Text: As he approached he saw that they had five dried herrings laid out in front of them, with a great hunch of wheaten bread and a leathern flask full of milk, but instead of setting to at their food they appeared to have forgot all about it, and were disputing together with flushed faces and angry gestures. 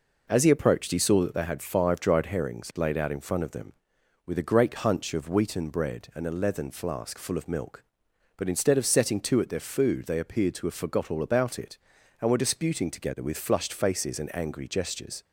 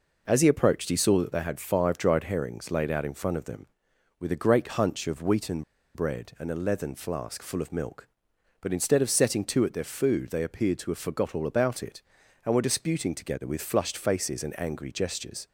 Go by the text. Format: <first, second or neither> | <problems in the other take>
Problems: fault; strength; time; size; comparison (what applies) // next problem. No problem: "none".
first | pauses between "wheaten" and "bread"; slight; at 5.6 s; 0.31 s long